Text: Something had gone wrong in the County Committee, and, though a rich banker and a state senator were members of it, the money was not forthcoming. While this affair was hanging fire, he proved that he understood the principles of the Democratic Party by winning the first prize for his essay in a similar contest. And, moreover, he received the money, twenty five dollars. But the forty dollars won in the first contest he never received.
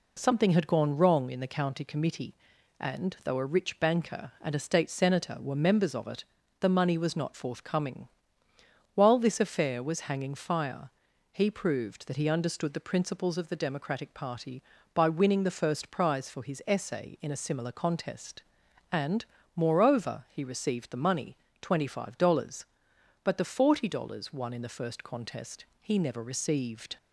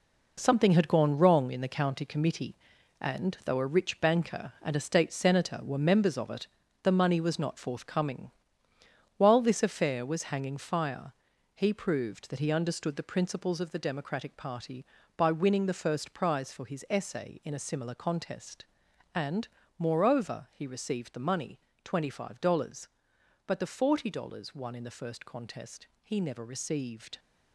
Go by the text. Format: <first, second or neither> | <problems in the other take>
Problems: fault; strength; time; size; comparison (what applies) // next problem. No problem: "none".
first | gets quieter; strong; throughout; 9.5 dB // pauses between "contest" and "he"; slight; at 25.8 s; 0.16 s long; slight in the first